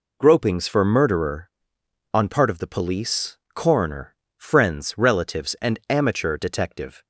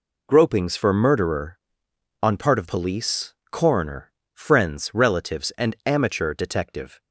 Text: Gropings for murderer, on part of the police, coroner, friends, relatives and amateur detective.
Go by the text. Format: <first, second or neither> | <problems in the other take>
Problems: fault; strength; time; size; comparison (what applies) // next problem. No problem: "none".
first | skips "the"; at 2.6 s